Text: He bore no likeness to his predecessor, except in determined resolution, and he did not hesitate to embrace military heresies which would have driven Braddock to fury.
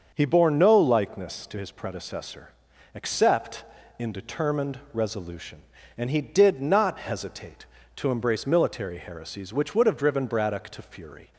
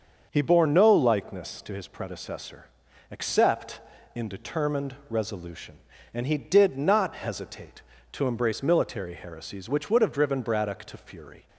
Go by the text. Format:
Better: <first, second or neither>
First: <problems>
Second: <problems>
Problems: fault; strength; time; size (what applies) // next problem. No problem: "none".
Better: neither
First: starts louder than the rest; until 1.1 s; 6.5 dB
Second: starts louder than the rest; until 1.3 s; 6.5 dB